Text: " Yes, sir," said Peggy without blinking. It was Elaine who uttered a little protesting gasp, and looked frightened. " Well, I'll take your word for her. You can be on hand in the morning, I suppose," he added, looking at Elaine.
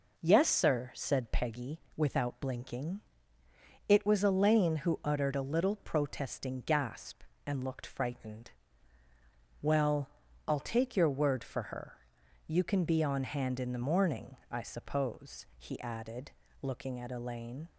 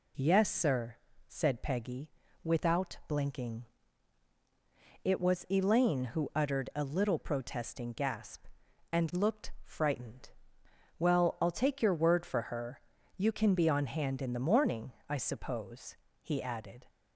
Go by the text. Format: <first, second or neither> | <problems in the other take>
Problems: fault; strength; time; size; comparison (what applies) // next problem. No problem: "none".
first | pauses between "Peggy" and "without"; slight; at 2.0 s; 0.32 s long; slight in the first // stops before "looking at Elaine"; at 16.8 s